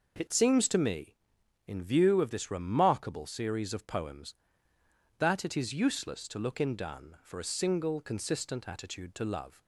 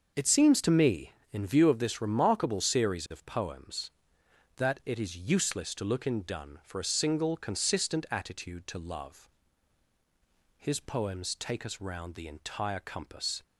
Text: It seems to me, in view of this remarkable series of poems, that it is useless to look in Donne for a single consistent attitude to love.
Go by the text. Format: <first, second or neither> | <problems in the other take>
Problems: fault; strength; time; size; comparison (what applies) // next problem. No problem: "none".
first | starts louder than the rest; until 1.3 s; 6.5 dB // goes on to say "His poems take us round the entire compass"; strong; from 10.5 s on; 2.8 s long